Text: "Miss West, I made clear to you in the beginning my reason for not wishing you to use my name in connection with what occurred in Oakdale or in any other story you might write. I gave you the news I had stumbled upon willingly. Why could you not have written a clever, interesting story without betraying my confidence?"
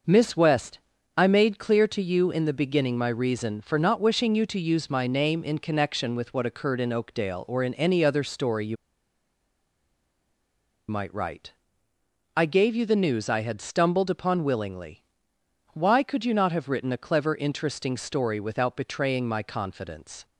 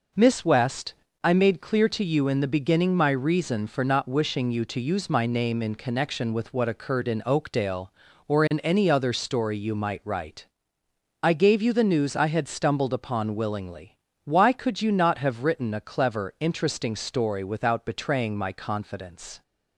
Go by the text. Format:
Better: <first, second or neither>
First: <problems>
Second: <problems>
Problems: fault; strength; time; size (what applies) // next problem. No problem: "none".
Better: second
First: starts louder than the rest; noticeable; until 1.4 s; 6 dB // pauses between "you" and "might"; strong; at 8.7 s; 2.1 s long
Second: none